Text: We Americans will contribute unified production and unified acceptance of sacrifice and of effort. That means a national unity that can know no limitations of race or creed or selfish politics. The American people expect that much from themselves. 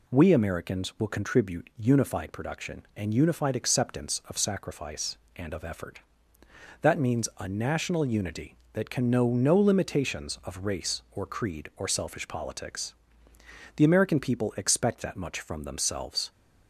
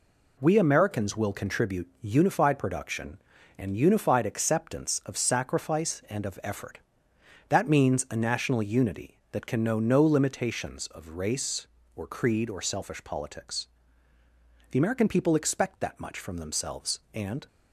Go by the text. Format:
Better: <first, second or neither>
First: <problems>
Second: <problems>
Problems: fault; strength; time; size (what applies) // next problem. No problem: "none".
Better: first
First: none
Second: goes on to say "And"; slight; from 17.1 s on; 0.32 s long